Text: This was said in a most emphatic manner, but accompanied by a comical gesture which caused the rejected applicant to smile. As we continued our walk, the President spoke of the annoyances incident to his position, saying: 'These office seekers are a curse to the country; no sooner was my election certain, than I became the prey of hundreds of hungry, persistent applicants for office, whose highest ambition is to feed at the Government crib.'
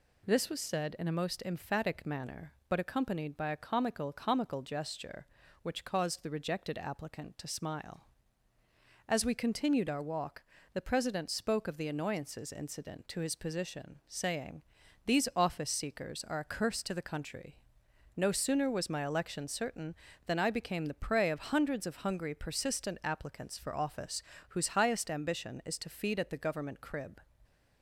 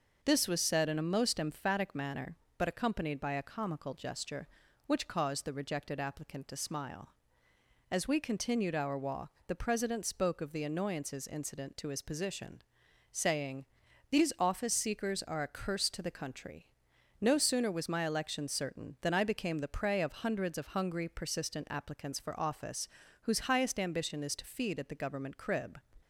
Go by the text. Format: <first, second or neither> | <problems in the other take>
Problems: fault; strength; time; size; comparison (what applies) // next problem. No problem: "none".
second | says "comical" twice; at 4.1 s